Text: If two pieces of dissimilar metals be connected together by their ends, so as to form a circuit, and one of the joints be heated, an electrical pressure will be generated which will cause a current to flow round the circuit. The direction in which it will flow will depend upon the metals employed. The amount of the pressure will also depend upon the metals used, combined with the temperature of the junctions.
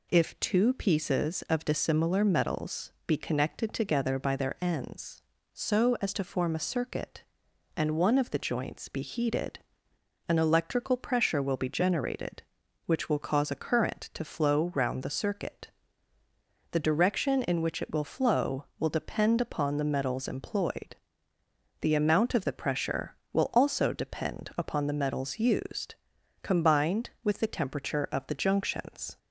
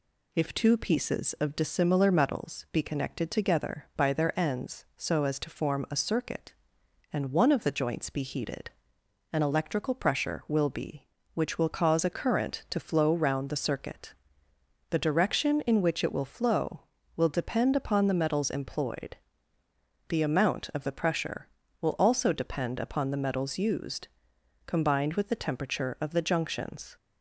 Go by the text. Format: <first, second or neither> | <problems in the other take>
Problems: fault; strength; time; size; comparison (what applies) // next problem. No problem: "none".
first | skips "generated"; at 11.1 s